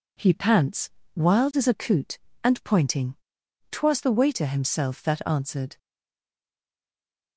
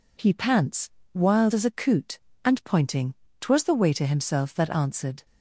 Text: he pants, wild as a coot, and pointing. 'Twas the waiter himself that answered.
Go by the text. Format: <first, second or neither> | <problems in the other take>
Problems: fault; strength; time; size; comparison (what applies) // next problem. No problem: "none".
second | stays silent after the last word; noticeable; from 5.7 s on; 1.6 s long